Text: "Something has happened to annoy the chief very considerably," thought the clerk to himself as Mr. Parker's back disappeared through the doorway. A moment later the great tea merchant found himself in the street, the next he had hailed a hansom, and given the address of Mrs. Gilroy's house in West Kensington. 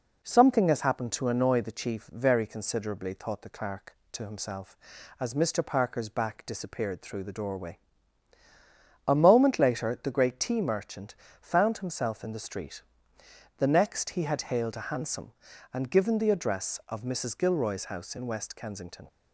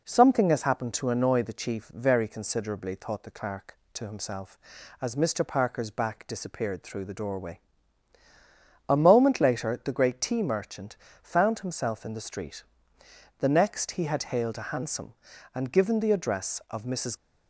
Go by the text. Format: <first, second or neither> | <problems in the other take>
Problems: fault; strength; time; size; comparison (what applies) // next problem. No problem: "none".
first | pauses between "merchant" and "found"; slight; at 10.9 s; 0.24 s long; slight in the first // stops before "Gilroy's house in West Kensington"; at 17.1 s